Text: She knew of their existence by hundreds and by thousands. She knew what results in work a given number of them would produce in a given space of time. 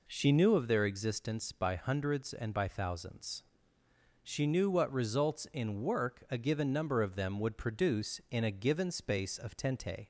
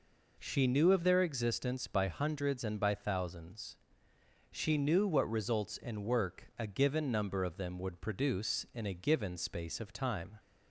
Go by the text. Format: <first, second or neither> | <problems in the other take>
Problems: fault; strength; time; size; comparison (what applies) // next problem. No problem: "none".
second | says "tente" for "time"; at 9.5 s